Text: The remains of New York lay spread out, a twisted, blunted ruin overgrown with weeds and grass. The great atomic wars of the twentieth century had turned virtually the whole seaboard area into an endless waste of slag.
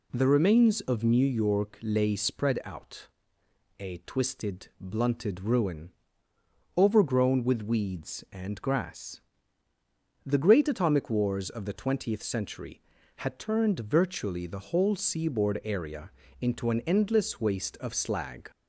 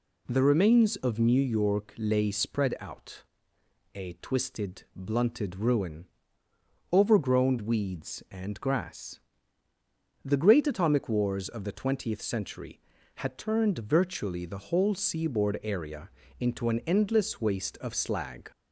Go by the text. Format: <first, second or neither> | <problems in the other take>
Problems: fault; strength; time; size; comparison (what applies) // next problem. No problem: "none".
first | pauses between "ruin" and "overgrown"; noticeable; at 6.0 s; 0.84 s long; noticeable in the first // skips "with"; at 7.5 s // pauses between "area" and "into"; slight; at 16.0 s; 0.30 s long; slight in the first